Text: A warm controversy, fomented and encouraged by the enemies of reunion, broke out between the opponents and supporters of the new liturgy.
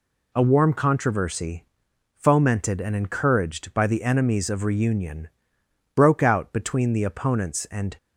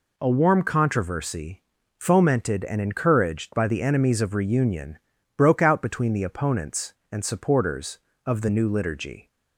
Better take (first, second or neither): second